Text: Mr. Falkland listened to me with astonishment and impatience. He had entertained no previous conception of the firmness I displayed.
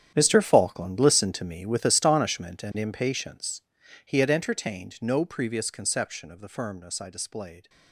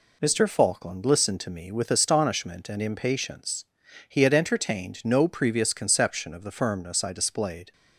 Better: second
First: gets quieter; strong; throughout; 15 dB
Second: none

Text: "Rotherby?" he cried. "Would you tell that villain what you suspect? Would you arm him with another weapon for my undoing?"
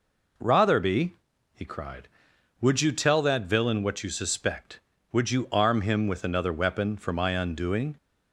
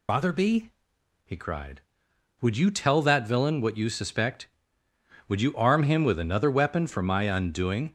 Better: first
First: none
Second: loses the start of "Rotherby"; at 0.0 s; 155 ms

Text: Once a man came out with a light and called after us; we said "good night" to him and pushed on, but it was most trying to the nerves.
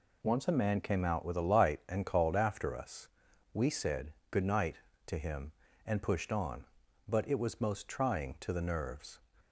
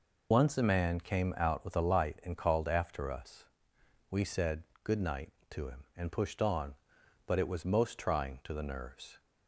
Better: first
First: pauses between "said" and "good"; slight; at 4.1 s; 0.16 s long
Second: loses the start of "Once"; at 0.3 s; 60 ms // pauses between "said" and "good"; slight; at 4.6 s; 0.18 s long

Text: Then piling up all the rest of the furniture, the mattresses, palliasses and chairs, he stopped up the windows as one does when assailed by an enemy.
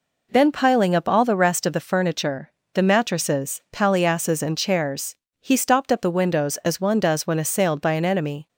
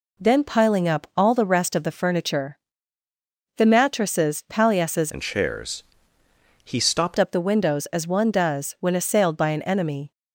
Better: first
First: none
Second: changes voice from "and" to "stopped"; from 5.1 to 7.1 s; 2.0 s long

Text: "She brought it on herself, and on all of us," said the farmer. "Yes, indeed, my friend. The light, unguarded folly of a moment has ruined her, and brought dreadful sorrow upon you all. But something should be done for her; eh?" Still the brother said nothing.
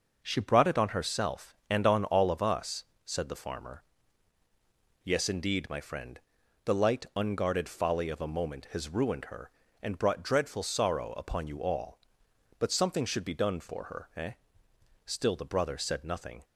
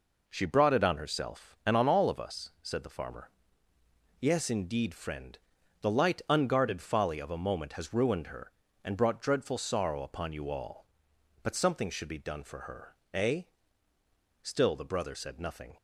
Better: first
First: none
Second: skips "my"; at 4.9 s

